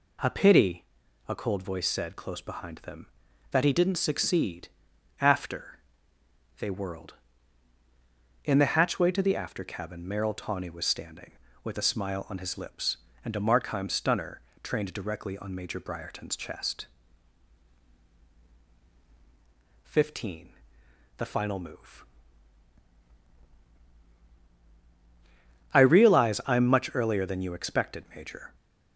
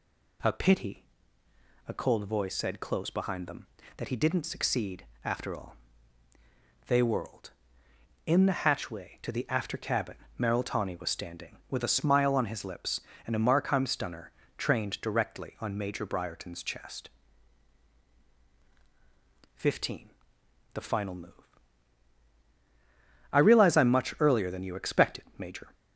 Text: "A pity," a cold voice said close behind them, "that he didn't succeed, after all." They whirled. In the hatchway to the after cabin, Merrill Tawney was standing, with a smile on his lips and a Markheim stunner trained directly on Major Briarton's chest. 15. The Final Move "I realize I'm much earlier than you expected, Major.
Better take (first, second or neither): second